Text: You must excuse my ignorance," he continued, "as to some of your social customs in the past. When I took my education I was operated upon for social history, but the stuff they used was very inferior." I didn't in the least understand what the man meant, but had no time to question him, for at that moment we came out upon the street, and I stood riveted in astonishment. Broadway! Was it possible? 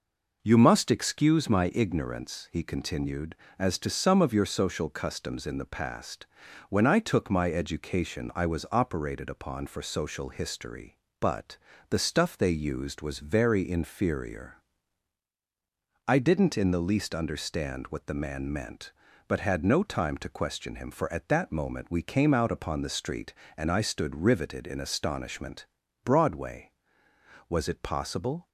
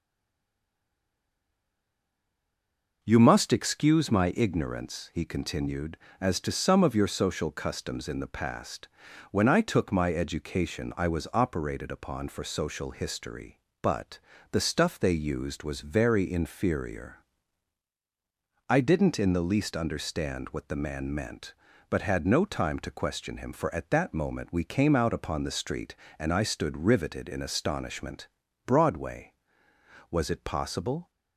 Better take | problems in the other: first | stays silent before the first word; strong; until 3.0 s; 3.0 s long // pauses between "but" and "the"; slight; at 14.1 s; 0.32 s long; slight in the first

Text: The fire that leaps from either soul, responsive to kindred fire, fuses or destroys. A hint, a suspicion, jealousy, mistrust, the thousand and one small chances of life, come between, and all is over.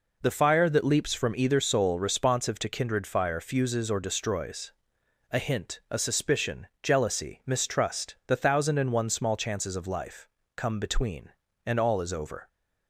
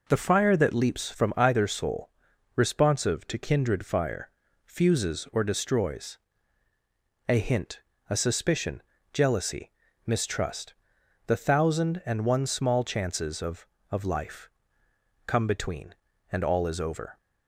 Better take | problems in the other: first | says "of" twice; at 13.9 s

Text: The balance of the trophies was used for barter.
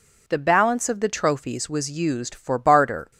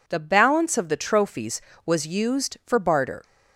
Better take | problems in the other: neither | none

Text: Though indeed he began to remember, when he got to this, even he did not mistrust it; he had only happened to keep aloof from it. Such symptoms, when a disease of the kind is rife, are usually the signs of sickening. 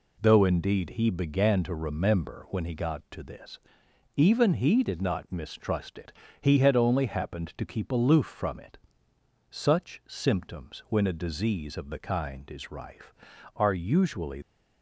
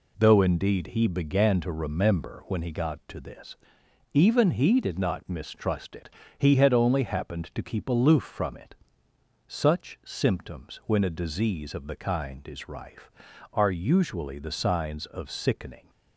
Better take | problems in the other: second | stops before "the signs of sickening"; at 14.4 s

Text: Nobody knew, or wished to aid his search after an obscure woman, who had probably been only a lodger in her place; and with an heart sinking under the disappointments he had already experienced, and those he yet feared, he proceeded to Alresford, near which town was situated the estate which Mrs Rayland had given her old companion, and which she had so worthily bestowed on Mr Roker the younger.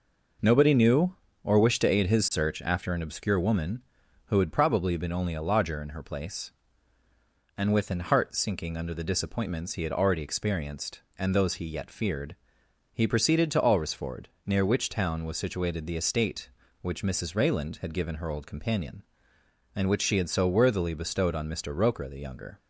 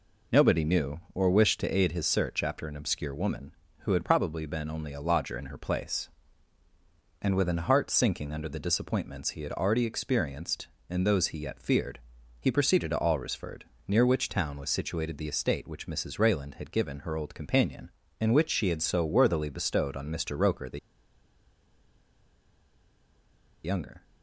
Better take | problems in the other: first | pauses between "the" and "younger"; strong; at 20.7 s; 2.8 s long

